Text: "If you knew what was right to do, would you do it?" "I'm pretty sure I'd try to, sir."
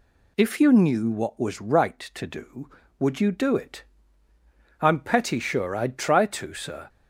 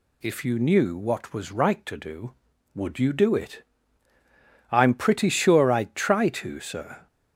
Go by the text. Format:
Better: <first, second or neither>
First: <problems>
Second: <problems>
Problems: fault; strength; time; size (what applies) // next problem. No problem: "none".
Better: second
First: says "petty" for "pretty"; at 4.9 s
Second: none